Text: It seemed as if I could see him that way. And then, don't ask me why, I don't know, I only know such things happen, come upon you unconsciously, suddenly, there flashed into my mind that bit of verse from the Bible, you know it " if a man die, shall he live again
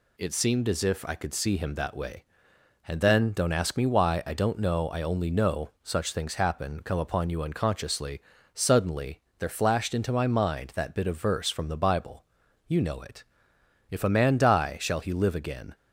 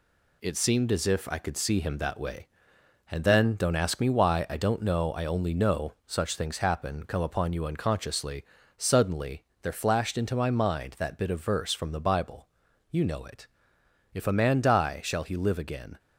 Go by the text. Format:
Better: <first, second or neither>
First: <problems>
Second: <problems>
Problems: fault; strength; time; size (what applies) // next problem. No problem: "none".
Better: first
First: none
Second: gets quieter; strong; throughout; 7.5 dB